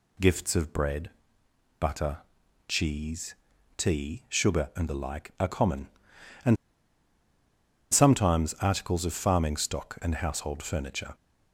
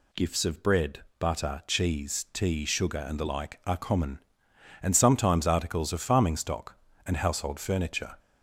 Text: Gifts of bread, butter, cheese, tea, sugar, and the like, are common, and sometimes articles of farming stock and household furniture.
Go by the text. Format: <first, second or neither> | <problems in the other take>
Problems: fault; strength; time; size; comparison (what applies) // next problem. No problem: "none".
second | pauses between "and" and "sometimes"; strong; at 6.5 s; 1.3 s long